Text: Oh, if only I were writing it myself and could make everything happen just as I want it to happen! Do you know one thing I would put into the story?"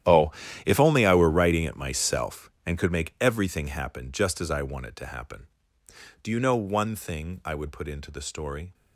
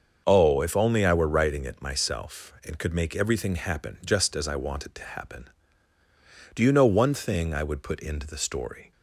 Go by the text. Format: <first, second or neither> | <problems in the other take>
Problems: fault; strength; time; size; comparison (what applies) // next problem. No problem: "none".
second | gets quieter; strong; throughout; 17 dB // starts louder than the rest; strong; until 1.4 s; 11.5 dB; also in the second